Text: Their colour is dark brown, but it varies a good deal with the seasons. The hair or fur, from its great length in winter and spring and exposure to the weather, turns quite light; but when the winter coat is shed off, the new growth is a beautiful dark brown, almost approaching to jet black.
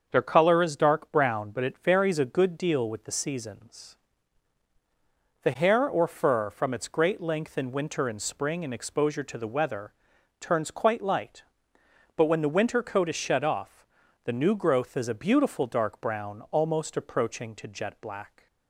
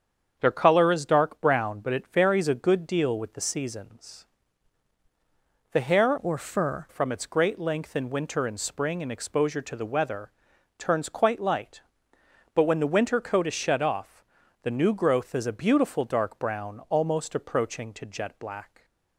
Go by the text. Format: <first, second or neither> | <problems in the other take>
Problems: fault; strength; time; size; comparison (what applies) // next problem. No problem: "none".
first | starts louder than the rest; strong; until 1.3 s; 7.5 dB; also in the first // changes voice from "or" to "fur"; from 6.1 to 6.8 s; 0.7 s long